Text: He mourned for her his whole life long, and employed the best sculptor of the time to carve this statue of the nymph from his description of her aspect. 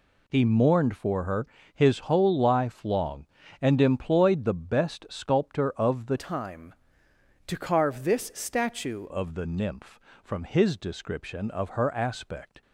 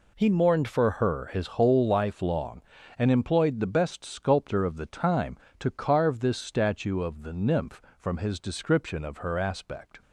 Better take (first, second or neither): second